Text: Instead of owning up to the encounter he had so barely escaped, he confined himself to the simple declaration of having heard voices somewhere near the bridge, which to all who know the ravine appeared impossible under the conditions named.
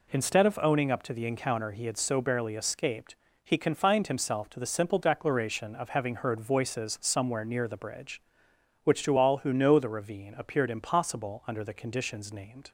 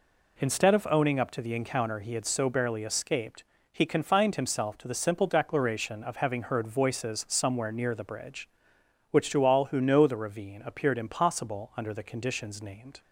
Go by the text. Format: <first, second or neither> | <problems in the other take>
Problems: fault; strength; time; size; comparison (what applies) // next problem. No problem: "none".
neither | none